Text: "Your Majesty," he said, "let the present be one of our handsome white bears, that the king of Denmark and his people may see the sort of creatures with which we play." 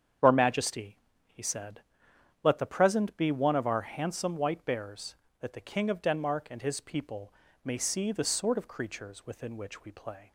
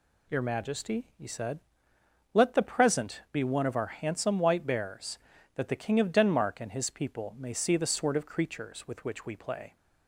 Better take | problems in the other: second | starts louder than the rest; strong; until 1.5 s; 8 dB // pauses between "people" and "may"; slight; at 7.3 s; 0.32 s long // says "within" for "with"; at 9.2 s

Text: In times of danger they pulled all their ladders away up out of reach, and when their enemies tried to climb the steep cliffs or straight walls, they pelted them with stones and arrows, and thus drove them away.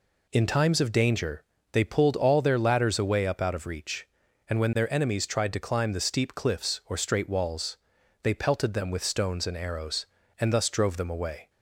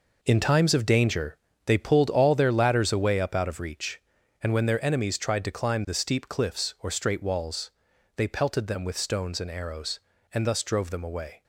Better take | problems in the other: first | gets quieter; strong; throughout; 10.5 dB // pauses between "danger" and "they"; slight; at 1.3 s; 0.30 s long; slight in the first

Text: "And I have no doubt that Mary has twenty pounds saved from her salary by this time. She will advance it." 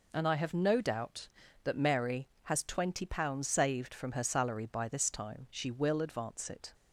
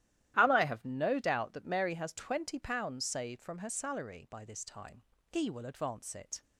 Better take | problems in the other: first | starts louder than the rest; strong; until 1.3 s; 13 dB // says "He" for "She"; at 5.3 s

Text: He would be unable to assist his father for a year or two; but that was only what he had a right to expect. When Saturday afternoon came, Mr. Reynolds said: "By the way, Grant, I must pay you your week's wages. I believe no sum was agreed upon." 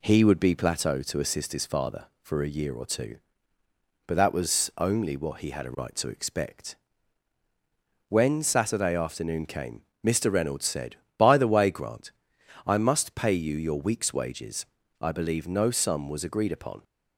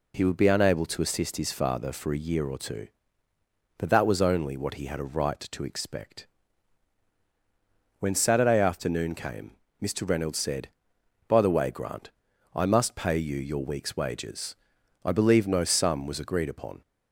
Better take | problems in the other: second | says "plateau" for "unable"; at 0.5 s

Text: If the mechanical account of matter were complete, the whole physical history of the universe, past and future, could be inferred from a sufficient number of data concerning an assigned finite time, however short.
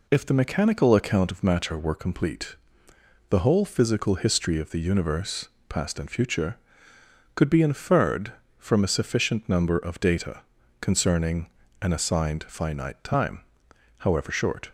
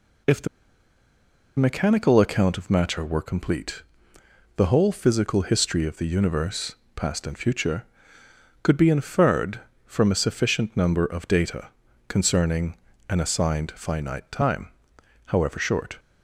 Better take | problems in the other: first | pauses between "the" and "mechanical"; at 0.4 s; 1.1 s long // pauses between "data" and "concerning"; at 11.6 s; 0.38 s long; also in the first // pauses between "concerning" and "an"; slight; at 12.7 s; 0.32 s long; slight in the first

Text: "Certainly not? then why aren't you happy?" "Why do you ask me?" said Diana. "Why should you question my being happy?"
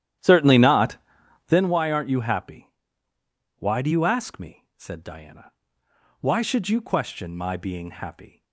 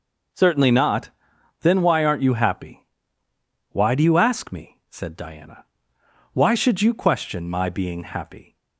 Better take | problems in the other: second | starts louder than the rest; strong; until 1.7 s; 11.5 dB

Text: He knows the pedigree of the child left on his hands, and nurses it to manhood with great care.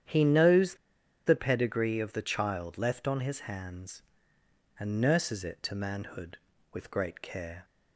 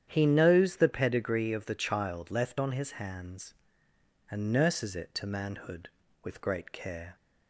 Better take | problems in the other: second | starts louder than the rest; strong; until 1.5 s; 9.5 dB; strong in the second // pauses between "knows" and "the"; noticeable; at 0.7 s; 0.50 s long

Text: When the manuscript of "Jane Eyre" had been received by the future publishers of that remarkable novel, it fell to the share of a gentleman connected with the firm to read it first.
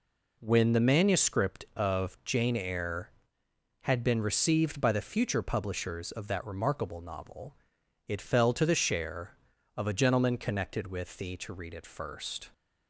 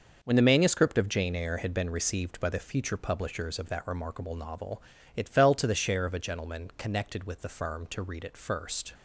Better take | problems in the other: second | skips "firm"; at 11.3 s

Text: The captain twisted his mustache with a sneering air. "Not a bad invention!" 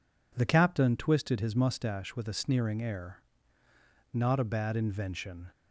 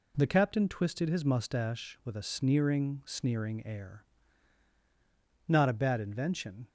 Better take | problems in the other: first | says "sneering" twice; at 3.0 s

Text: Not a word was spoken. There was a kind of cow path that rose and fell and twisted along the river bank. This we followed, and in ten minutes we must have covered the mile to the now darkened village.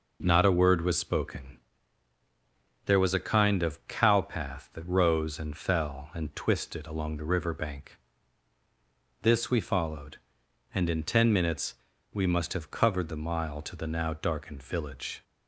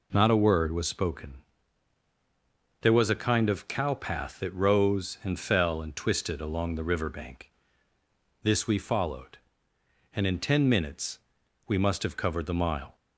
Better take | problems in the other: first | pauses between "minutes" and "we"; noticeable; at 11.1 s; 0.48 s long; also in the first // stops before "to the now darkened village"; at 12.9 s

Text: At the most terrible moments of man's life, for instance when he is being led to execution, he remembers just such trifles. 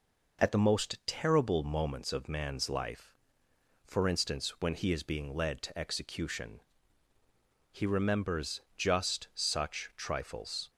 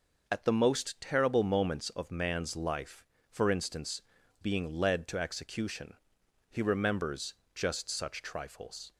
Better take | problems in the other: first | skips "when he is"; at 4.2 s // pauses between "remembers" and "just"; slight; at 7.3 s; 0.20 s long

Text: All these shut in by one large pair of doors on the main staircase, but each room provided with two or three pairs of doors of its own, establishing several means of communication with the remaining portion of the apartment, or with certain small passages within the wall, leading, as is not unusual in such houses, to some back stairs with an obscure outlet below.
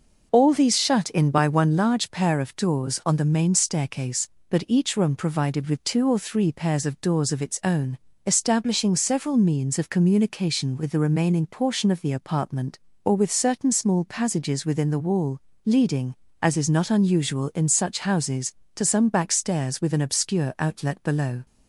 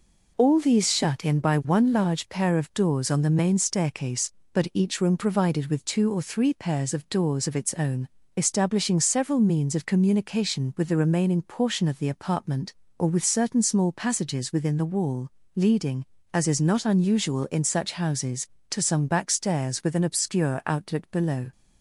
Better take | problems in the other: neither | none

